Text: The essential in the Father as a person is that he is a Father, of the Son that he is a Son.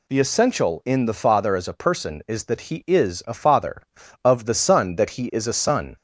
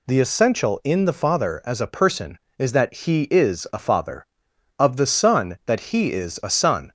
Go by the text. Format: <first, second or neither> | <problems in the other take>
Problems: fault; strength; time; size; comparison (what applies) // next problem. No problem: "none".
neither | none